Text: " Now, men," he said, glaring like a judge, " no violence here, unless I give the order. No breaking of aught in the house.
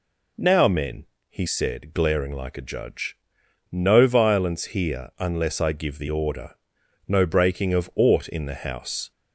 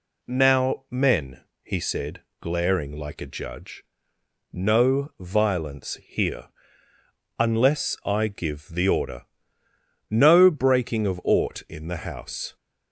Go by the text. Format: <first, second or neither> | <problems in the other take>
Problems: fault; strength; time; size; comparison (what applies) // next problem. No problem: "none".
neither | none